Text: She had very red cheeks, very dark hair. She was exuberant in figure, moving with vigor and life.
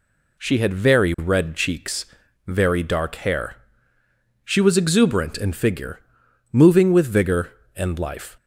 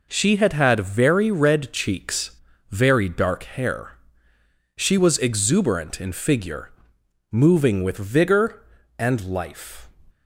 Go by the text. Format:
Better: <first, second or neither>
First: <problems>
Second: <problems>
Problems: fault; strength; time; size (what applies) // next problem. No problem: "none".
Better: first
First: none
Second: says "had" twice; at 0.5 s